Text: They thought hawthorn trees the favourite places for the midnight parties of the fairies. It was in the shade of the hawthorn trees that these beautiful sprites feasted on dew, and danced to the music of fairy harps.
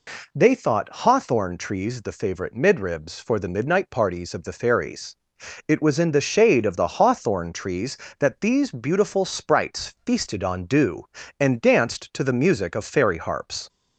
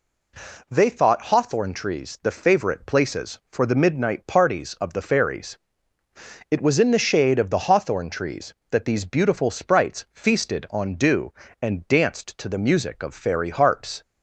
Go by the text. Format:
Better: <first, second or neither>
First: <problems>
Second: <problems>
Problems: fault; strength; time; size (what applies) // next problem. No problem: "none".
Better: second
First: says "midribs" for "places"; at 2.5 s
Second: none